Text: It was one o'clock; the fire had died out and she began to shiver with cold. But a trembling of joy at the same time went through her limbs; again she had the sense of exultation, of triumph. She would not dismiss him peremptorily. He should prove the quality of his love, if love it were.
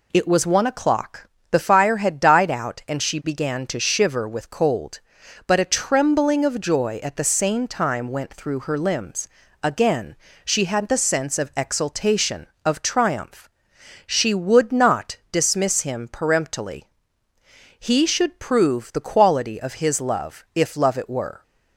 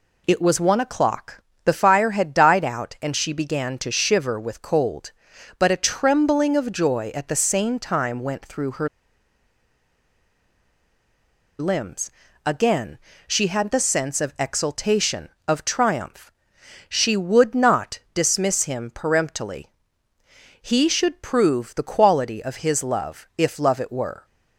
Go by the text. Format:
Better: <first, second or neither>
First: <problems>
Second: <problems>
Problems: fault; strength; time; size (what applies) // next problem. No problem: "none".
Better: first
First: pauses between "again" and "she"; slight; at 10.1 s; 0.30 s long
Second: pauses between "her" and "limbs"; strong; at 8.8 s; 2.7 s long // pauses between "again" and "she"; slight; at 12.9 s; 0.30 s long